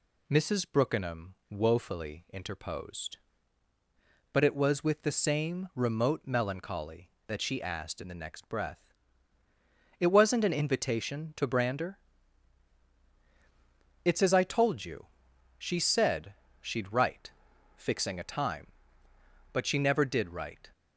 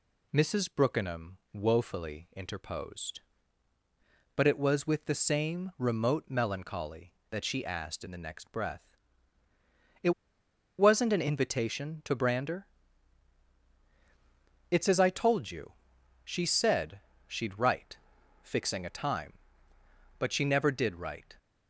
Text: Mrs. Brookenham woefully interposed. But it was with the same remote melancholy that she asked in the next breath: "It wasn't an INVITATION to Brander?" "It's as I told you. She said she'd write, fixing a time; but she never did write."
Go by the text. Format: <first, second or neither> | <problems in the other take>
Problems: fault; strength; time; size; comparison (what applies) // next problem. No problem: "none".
first | pauses between "Brookenham" and "woefully"; slight; at 1.3 s; 0.18 s long; slight in the first // pauses between "It" and "wasn't"; noticeable; at 10.1 s; 0.68 s long // pauses between "said" and "she'd"; slight; at 16.9 s; 0.26 s long; slight in the first